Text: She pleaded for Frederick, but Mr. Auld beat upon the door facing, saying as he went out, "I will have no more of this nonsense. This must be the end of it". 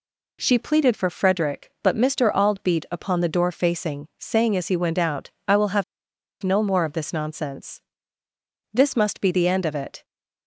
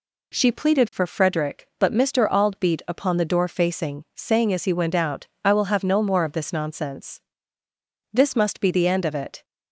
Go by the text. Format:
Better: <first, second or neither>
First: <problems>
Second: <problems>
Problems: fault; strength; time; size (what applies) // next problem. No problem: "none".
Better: second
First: pauses between "have" and "no"; noticeable; at 5.8 s; 0.58 s long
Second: none